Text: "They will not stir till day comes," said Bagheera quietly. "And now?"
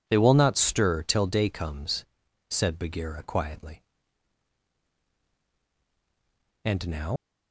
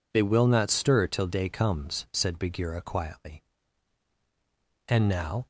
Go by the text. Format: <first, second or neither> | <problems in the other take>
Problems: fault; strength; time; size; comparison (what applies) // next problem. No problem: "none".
second | leaves "now" unfinished; at 7.1 s; 130 ms